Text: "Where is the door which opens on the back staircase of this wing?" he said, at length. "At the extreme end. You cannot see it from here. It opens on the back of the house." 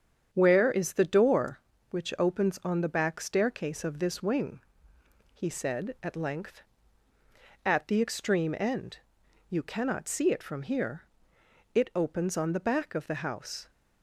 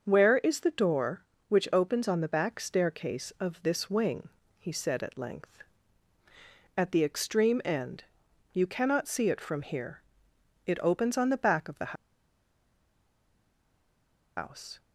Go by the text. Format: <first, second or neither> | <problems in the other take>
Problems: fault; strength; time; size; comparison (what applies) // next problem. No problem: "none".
first | starts louder than the rest; until 1.0 s; 6.5 dB; strong in the first // pauses between "the" and "house"; strong; at 11.9 s; 2.4 s long